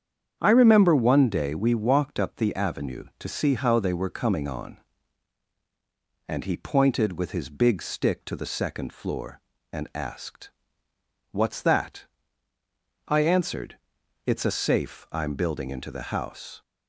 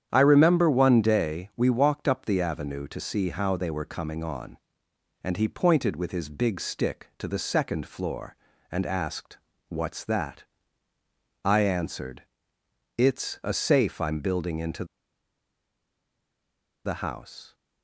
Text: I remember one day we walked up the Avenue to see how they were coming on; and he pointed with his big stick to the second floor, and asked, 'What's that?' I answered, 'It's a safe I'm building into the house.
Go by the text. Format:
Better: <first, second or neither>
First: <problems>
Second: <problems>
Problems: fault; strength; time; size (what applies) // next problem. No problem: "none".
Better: first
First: starts louder than the rest; strong; until 1.4 s; 8 dB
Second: starts louder than the rest; strong; until 1.1 s; 9 dB // pauses between "into" and "the"; strong; at 14.8 s; 2.0 s long